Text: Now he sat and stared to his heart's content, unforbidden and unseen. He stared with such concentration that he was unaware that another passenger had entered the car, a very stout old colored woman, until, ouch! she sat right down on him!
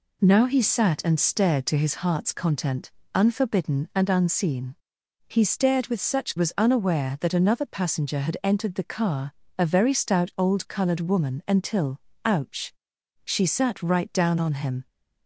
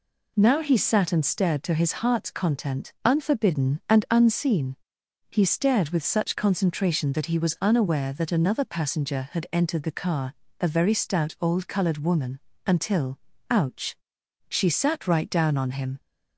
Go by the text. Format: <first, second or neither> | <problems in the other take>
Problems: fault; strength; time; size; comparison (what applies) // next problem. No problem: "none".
second | skips "concentration that he"; at 6.3 s